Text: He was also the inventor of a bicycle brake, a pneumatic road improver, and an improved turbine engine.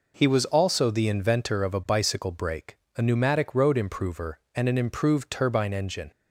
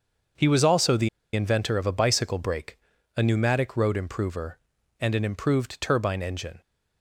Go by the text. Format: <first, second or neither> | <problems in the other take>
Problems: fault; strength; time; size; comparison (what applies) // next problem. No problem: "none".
first | starts louder than the rest; until 1.6 s; 6.5 dB // pauses between "the" and "inventor"; slight; at 1.0 s; 0.25 s long